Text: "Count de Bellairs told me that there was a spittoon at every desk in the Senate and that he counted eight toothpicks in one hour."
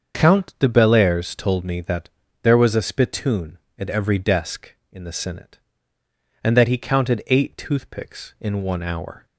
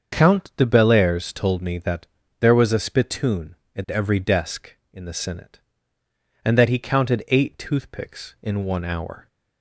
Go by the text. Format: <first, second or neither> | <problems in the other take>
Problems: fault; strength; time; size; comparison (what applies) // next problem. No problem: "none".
neither | starts louder than the rest; the same in both // pauses between "that" and "there"; slight; the same in both